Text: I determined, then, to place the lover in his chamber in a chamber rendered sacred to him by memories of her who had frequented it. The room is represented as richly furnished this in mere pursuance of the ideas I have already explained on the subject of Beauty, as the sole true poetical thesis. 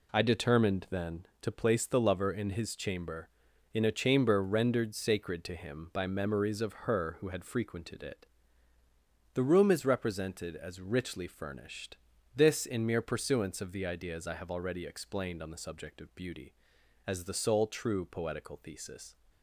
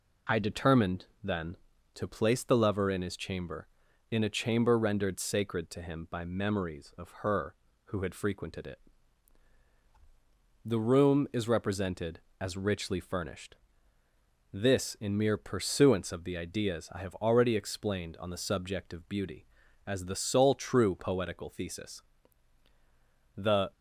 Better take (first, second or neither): first